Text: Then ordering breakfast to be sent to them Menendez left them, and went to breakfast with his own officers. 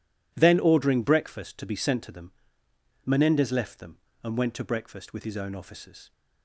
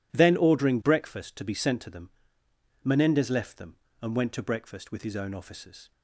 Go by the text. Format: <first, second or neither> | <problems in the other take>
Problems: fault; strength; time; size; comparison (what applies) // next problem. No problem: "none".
neither | pauses between "them" and "Menendez"; noticeable; the same in both